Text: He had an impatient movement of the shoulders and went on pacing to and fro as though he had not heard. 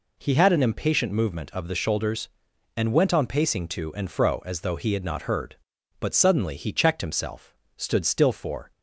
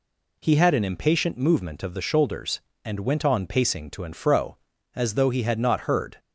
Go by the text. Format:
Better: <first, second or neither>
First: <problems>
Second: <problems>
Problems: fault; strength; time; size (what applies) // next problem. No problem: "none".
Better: second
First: goes on to say "But suddenly he checked himself stood still for"; strong; from 5.9 s on; 2.7 s long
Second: none